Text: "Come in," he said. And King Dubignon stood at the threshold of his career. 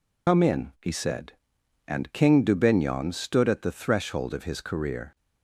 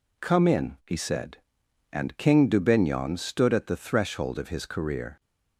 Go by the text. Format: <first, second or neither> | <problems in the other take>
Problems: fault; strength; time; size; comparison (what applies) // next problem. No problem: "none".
second | loses the start of "Come"; at 0.2 s; 115 ms